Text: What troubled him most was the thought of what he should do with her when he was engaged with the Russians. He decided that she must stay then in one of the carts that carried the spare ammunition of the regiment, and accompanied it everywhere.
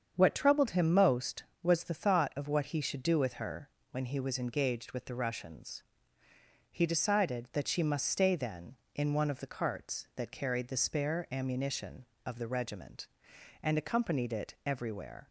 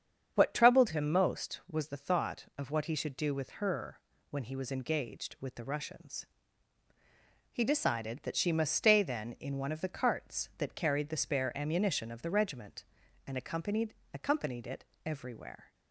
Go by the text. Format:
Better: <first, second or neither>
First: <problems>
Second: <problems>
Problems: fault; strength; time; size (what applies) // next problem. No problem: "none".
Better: first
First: starts louder than the rest; strong; until 1.1 s; 7.5 dB // pauses between "her" and "when"; slight; at 3.6 s; 0.24 s long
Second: starts louder than the rest; strong; until 1.3 s; 7.5 dB // pauses between "her" and "when"; slight; at 3.9 s; 0.32 s long // says "accompanied" twice; at 14.1 s // pauses between "it" and "everywhere"; slight; at 14.8 s; 0.20 s long